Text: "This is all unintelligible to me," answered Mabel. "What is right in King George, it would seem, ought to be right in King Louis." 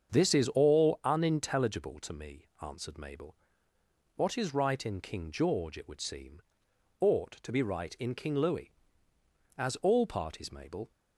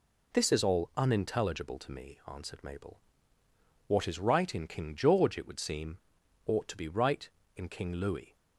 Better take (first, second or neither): second